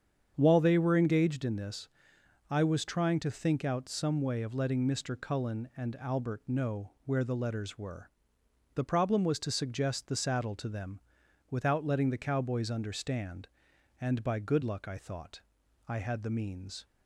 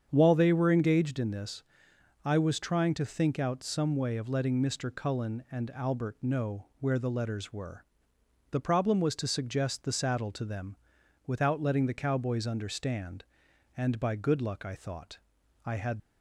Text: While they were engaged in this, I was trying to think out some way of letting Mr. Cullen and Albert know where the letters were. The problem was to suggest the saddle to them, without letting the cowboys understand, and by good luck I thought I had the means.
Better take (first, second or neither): first